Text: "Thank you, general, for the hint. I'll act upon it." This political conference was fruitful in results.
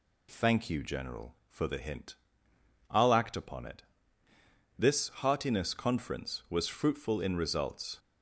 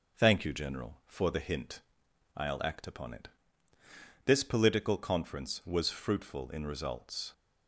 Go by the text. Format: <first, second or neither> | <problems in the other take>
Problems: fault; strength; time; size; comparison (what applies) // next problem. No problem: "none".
second | says "heartiness" for "political"; at 5.0 s